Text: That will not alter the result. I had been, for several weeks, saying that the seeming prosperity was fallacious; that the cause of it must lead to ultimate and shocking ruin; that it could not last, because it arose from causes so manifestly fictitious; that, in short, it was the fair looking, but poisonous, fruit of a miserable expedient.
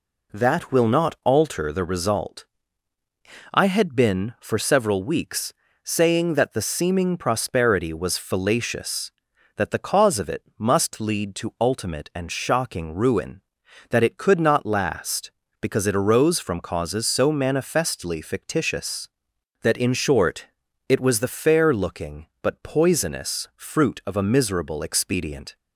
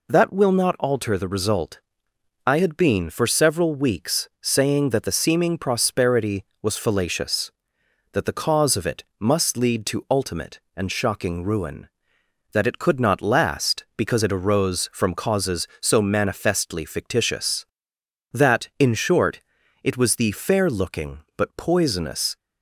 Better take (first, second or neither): first